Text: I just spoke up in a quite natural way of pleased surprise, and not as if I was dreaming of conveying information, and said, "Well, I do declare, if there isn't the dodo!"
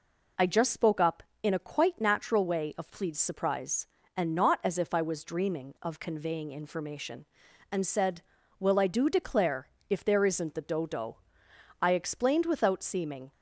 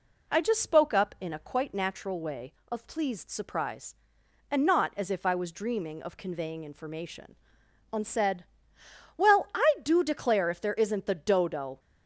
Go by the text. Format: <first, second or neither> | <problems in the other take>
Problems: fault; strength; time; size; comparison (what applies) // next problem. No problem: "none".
second | goes on to say "I explained without seeming"; from 11.7 s on; 1.5 s long